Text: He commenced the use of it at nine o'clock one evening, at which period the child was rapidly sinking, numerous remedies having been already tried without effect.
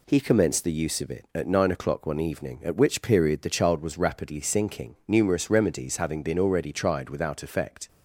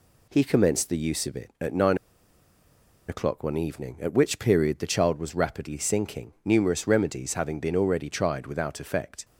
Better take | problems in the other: first | pauses between "nine" and "o'clock"; at 1.9 s; 1.1 s long

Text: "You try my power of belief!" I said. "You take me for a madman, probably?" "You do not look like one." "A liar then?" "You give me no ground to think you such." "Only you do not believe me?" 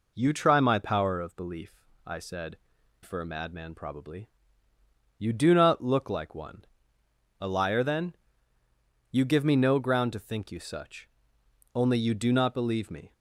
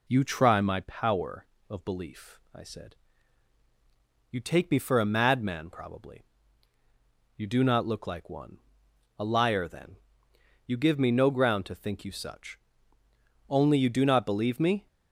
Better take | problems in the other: second | skips "You take me"; at 2.7 s

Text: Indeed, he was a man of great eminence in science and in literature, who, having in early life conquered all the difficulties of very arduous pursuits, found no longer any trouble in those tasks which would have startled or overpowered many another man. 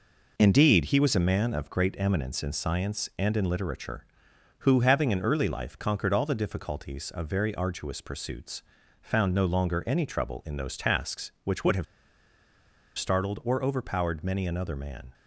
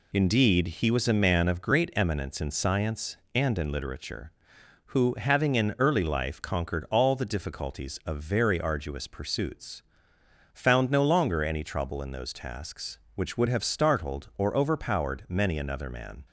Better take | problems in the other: second | pauses between "have" and "startled"; at 11.8 s; 1.1 s long

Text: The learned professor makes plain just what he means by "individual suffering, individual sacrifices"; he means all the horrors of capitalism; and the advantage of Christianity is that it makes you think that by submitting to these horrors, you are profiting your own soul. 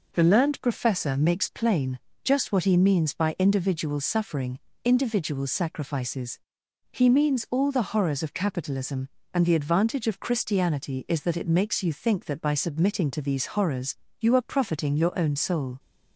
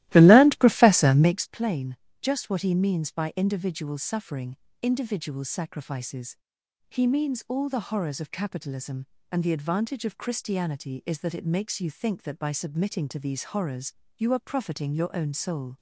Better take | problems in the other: first | starts louder than the rest; strong; until 1.4 s; 16 dB // pauses between "plain" and "just"; slight; at 1.9 s; 0.24 s long; slight in the first

